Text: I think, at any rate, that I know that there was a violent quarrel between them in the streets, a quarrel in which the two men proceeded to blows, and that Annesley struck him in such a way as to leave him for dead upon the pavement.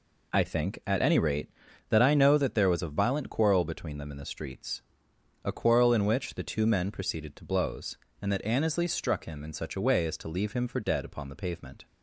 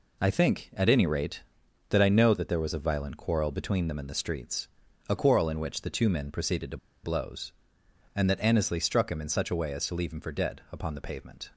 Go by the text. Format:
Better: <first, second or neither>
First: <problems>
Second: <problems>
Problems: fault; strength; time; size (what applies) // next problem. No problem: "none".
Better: first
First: none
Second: pauses between "to" and "blows"; slight; at 6.7 s; 0.27 s long